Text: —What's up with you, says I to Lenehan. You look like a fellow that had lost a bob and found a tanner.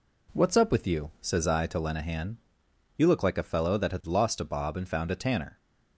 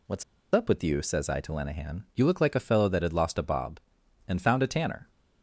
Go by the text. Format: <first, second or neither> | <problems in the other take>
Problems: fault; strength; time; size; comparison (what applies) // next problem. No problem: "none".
first | pauses between "What's" and "up"; slight; at 0.2 s; 0.29 s long